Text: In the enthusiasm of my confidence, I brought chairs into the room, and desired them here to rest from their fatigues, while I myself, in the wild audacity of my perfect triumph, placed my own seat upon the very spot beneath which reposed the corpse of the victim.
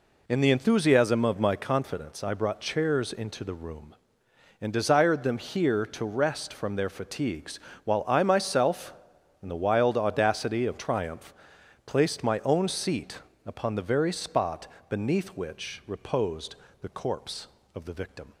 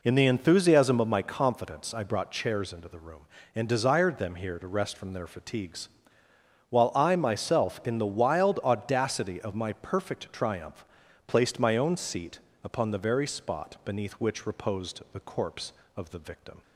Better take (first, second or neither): second